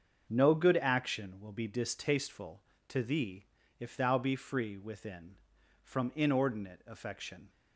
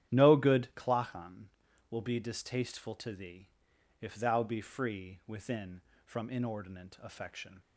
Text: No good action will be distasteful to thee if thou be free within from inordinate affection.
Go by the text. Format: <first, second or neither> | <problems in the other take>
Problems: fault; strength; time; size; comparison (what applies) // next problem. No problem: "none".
first | starts louder than the rest; strong; until 1.1 s; 11 dB; also in the first // says "clachan" for "action"; at 0.7 s // pauses between "thee" and "if"; noticeable; at 3.4 s; 0.50 s long; slight in the first